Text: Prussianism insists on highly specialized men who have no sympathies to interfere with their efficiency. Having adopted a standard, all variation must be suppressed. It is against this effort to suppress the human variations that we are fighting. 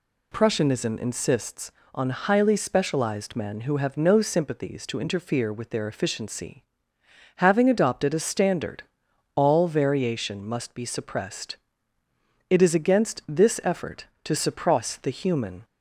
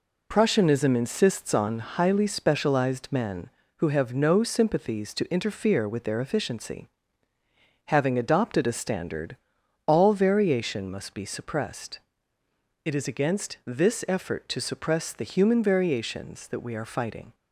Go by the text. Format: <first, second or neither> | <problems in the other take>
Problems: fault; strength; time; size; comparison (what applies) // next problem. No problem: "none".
second | stops before "variations that we are fighting"; at 15.6 s